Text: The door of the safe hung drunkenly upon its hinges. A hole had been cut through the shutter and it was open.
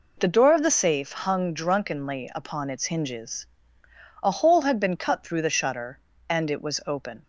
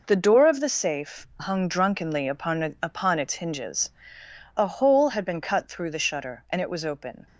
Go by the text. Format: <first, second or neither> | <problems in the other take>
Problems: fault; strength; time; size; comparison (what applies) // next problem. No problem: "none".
first | says "upon" twice; at 2.8 s